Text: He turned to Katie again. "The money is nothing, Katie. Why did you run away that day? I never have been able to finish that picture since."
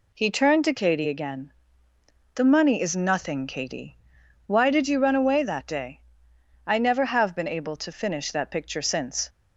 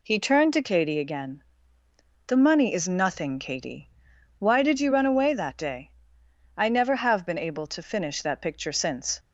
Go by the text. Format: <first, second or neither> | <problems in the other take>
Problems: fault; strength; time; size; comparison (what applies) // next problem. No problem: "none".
neither | none